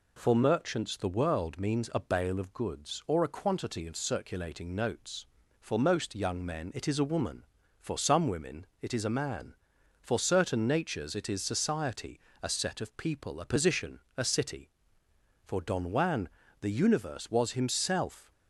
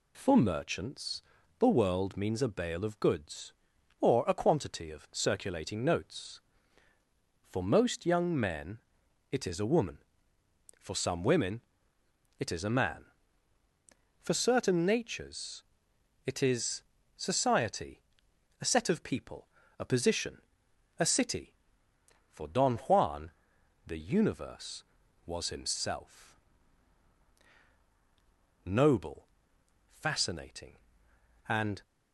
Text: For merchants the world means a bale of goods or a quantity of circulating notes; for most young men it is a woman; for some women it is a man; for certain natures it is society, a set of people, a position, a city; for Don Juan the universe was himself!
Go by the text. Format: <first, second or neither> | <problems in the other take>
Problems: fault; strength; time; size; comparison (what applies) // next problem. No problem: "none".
first | pauses between "merchants" and "the"; at 1.2 s; 0.38 s long // pauses between "men" and "it"; noticeable; at 8.7 s; 0.50 s long // pauses between "women" and "it"; noticeable; at 11.5 s; 0.80 s long; slight in the first // pauses between "natures" and "it"; noticeable; at 15.6 s; 0.64 s long // pauses between "is" and "society"; slight; at 16.8 s; 0.34 s long // pauses between "Juan" and "the"; noticeable; at 23.2 s; 0.56 s long; slight in the first // goes on to say "Noble fascinating and"; strong; from 28.6 s on; 3.1 s long